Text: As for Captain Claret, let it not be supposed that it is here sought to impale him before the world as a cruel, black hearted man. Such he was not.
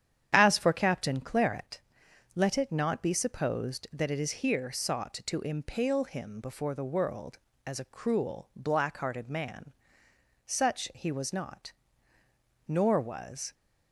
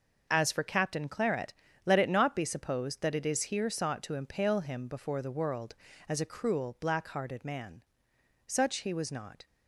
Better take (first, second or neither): second